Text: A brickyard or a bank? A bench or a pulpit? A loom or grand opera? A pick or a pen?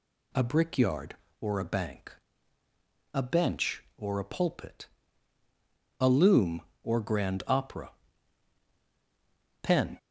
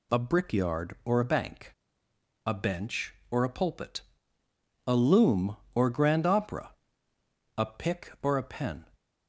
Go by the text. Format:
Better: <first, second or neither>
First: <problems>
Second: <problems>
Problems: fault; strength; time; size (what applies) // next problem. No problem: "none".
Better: second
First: skips "A pick or a"; at 8.7 s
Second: none